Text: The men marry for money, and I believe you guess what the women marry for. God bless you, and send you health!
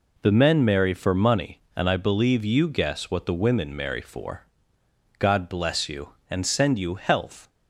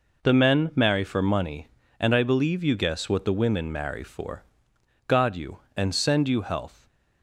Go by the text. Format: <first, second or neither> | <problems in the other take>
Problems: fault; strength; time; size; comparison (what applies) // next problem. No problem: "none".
first | skips "bless"; at 5.3 s